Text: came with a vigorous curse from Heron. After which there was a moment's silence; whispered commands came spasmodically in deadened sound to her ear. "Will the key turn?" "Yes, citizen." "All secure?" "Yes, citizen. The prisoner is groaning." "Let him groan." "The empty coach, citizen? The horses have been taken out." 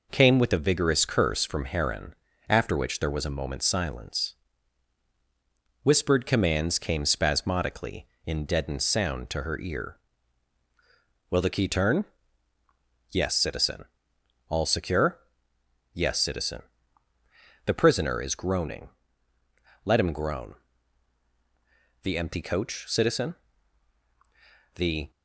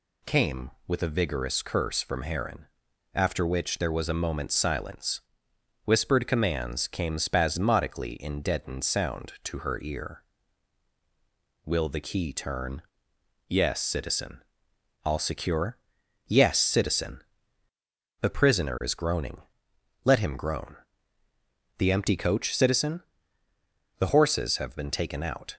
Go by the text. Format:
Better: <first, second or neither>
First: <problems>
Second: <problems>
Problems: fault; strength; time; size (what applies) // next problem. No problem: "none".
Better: second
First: stops before "horses have been taken out"; at 25.1 s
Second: none